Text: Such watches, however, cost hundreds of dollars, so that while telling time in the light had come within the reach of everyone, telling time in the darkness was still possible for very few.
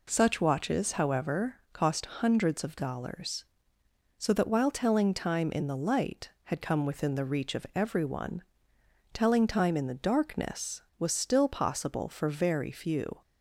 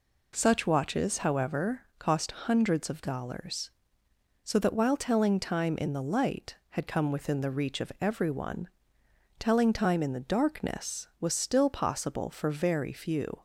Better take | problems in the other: neither | none

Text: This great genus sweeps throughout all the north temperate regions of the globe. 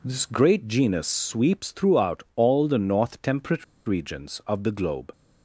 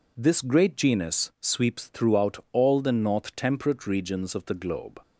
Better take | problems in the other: second | pauses between "temperate" and "regions"; slight; at 3.6 s; 0.22 s long

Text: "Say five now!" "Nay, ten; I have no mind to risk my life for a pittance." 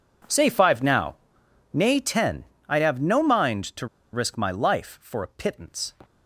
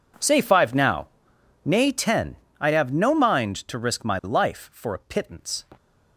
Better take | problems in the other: second | pauses between "to" and "risk"; slight; at 3.8 s; 0.25 s long

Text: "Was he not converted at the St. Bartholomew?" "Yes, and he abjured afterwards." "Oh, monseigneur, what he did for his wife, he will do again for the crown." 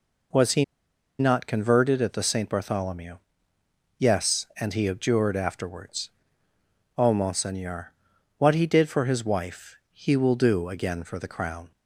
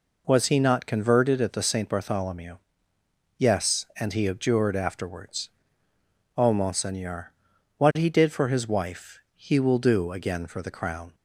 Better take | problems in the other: second | pauses between "he" and "not"; noticeable; at 0.6 s; 0.54 s long

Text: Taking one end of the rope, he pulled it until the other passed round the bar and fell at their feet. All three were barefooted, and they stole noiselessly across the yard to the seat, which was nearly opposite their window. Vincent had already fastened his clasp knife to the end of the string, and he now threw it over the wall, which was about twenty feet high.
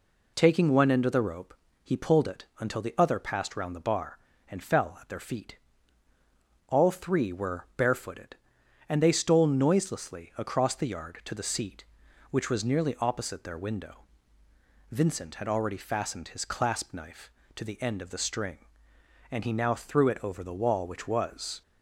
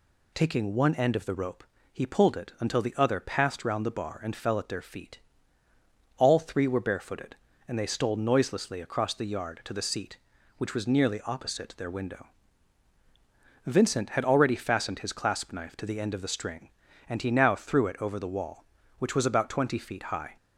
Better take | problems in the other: second | stops before "about twenty feet high"; at 21.6 s

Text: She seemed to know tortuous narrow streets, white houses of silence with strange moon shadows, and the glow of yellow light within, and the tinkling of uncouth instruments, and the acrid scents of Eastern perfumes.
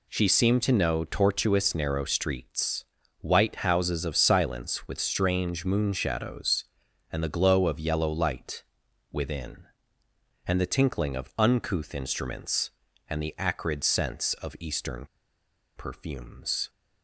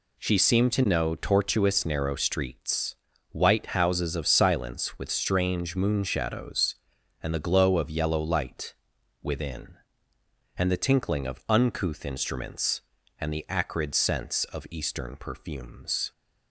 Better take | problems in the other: second | pauses between "light" and "within"; noticeable; at 8.6 s; 0.50 s long; noticeable in the second // pauses between "Eastern" and "perfumes"; noticeable; at 15.0 s; 0.71 s long

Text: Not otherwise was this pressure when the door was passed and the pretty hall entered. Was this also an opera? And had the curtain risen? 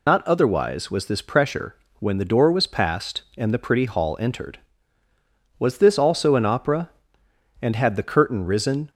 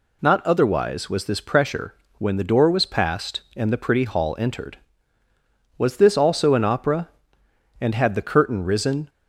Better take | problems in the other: second | loses the start of "Not"; at 0.0 s; 45 ms // pauses between "pressure" and "when"; slight; at 1.7 s; 0.24 s long; slight in the second

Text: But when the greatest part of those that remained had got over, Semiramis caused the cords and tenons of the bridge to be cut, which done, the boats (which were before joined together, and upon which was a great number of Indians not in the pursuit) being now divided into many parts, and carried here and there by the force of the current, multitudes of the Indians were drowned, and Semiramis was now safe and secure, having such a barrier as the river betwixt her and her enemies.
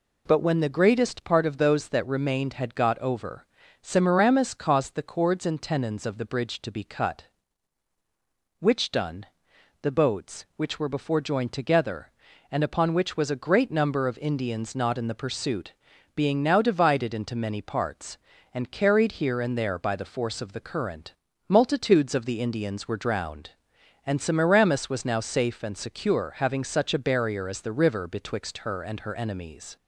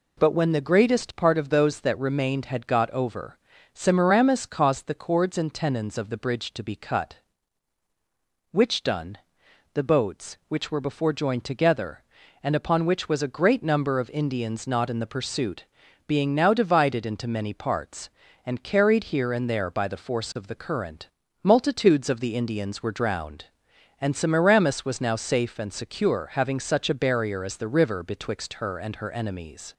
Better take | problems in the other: neither | none

